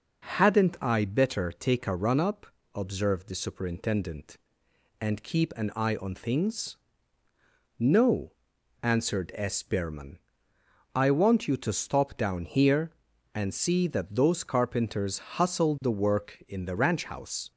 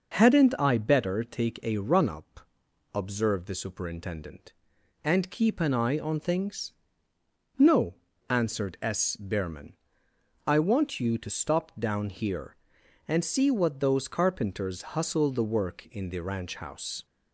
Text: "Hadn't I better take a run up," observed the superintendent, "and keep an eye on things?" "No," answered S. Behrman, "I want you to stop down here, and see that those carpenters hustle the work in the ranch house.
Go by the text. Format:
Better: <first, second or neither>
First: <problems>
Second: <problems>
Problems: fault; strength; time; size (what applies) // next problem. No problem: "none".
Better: first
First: none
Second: says "what" for "that"; at 13.4 s // pauses between "carpenters" and "hustle"; slight; at 14.8 s; 0.18 s long